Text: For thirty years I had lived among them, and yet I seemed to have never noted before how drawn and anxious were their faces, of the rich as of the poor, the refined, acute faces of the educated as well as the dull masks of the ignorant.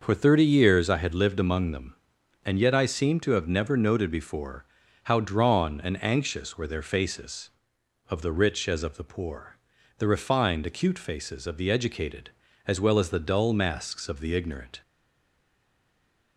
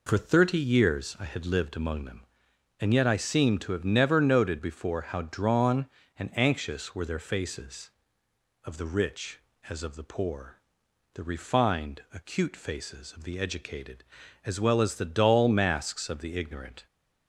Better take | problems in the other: second | starts louder than the rest; noticeable; until 1.0 s; 6 dB // pauses between "before" and "how"; at 4.6 s; 0.40 s long // stays silent after the last word; noticeable; from 14.8 s on; 1.5 s long

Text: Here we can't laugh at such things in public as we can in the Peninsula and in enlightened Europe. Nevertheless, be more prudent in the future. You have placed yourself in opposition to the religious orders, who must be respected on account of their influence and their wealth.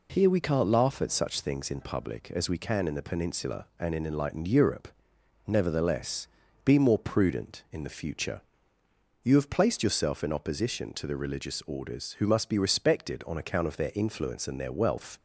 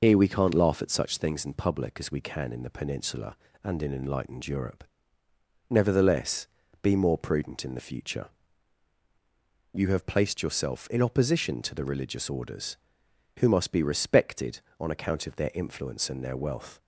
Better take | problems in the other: first | loses the start of "Here"; at 0.0 s; 55 ms

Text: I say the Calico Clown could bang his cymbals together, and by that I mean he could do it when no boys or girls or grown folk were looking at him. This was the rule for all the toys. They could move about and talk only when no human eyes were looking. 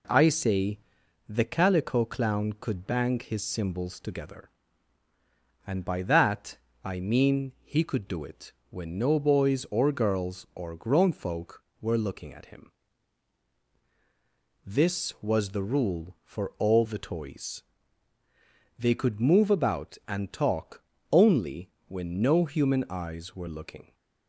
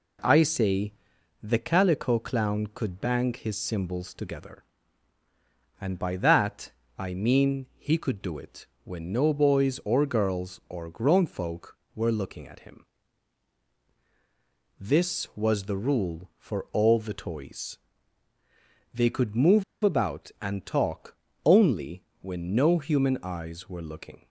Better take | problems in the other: first | pauses between "say" and "the"; noticeable; at 0.9 s; 0.50 s long; noticeable in the first // pauses between "that" and "I"; slight; at 6.7 s; 0.26 s long; slight in the first // pauses between "it" and "when"; slight; at 8.6 s; 0.18 s long; slight in the first // pauses between "move" and "about"; slight; at 19.6 s; 0.18 s long // pauses between "talk" and "only"; slight; at 21.1 s; 0.28 s long; slight in the first // pauses between "only" and "when"; slight; at 22.0 s; 0.18 s long; slight in the first

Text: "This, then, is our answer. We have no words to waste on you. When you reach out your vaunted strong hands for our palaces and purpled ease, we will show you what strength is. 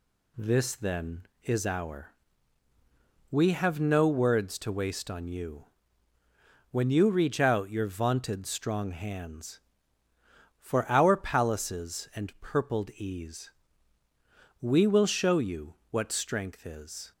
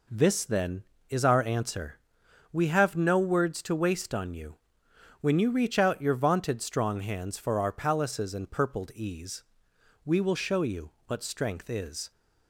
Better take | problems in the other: second | skips "answer"; at 2.7 s // pauses between "you" and "what"; slight; at 15.7 s; 0.18 s long; slight in the second

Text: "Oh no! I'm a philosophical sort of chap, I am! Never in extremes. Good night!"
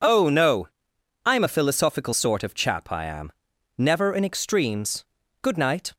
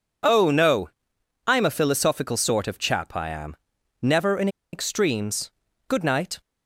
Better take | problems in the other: first | pauses between "in" and "extremes"; slight; at 4.4 s; 0.25 s long

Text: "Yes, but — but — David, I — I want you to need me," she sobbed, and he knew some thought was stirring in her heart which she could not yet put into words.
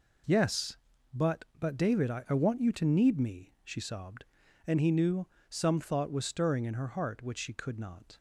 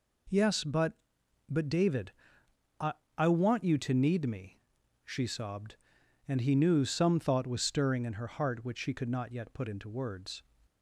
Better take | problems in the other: second | pauses between "knew" and "some"; slight; at 5.2 s; 0.24 s long // stops before "yet put into words"; at 8.1 s

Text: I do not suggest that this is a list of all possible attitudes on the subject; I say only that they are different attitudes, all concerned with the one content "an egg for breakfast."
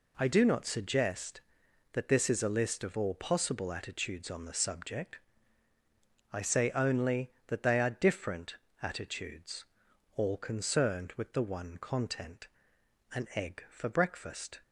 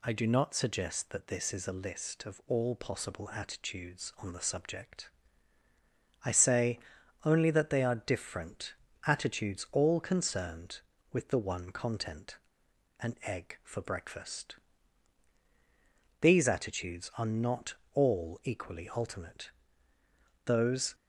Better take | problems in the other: first | pauses between "say" and "only"; noticeable; at 6.7 s; 0.46 s long // pauses between "different" and "attitudes"; slight; at 8.7 s; 0.32 s long; slight in the first // pauses between "content" and "an"; noticeable; at 12.3 s; 0.66 s long; noticeable in the first // goes on to say "These attitudes are not all equally ultimate Those"; strong; from 16.2 s on; 4.7 s long

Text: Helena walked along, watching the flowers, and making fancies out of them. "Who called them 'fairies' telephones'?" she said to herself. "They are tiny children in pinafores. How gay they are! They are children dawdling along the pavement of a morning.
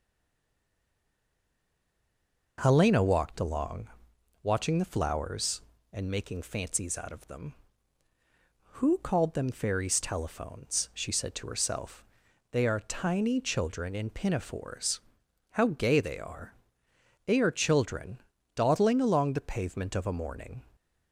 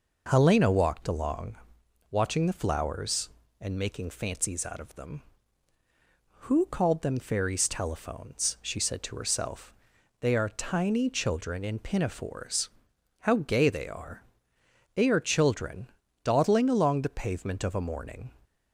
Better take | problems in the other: second | stays silent before the first word; strong; until 2.5 s; 2.5 s long // pauses between "children" and "dawdling"; at 18.1 s; 0.38 s long; also in the second

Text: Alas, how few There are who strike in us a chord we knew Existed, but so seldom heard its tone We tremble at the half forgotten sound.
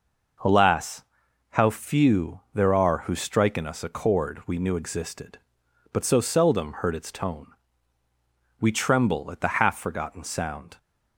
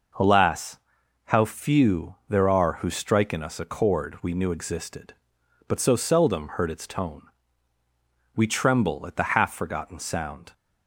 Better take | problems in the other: neither | pauses between "tone" and "We"; the same in both

